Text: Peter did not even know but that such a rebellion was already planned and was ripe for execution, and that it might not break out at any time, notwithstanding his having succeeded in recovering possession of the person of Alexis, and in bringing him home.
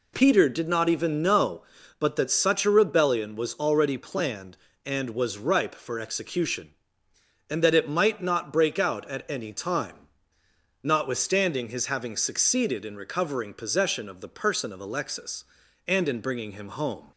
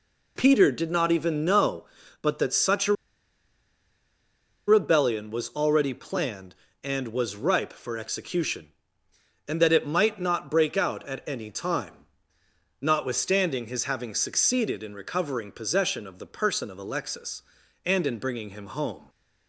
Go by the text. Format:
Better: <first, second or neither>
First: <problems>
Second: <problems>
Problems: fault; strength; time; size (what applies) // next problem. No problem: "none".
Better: first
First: none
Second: pauses between "a" and "rebellion"; strong; at 2.9 s; 1.7 s long